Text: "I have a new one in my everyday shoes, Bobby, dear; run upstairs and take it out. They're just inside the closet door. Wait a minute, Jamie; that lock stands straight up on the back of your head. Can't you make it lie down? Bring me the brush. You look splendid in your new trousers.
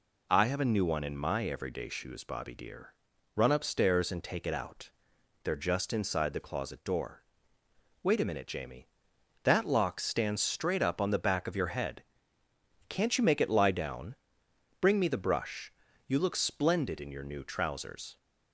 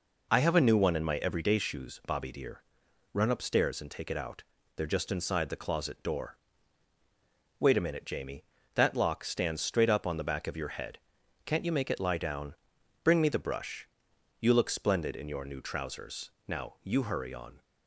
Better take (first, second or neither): first